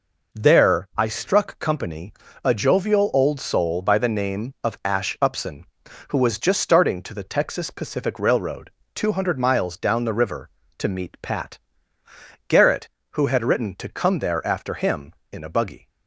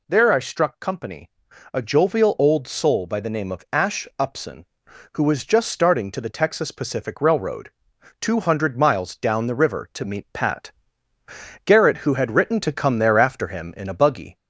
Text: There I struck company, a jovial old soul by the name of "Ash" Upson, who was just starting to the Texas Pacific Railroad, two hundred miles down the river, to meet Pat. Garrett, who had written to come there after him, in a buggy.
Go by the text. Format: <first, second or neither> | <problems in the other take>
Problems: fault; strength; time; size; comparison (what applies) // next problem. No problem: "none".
first | gets louder; slight; throughout; 2.5 dB